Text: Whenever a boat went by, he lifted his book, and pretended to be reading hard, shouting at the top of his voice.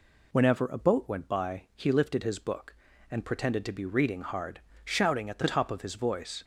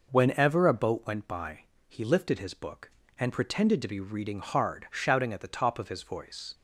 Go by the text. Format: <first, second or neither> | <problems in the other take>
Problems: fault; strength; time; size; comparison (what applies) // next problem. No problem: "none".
neither | none